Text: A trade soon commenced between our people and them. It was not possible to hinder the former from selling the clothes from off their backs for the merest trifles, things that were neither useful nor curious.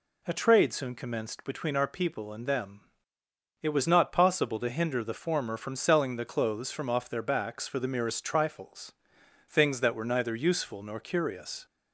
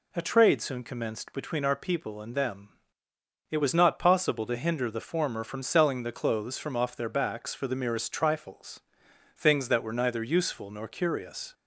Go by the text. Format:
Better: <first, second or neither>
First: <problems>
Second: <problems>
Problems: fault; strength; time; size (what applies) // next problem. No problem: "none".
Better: neither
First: none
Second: none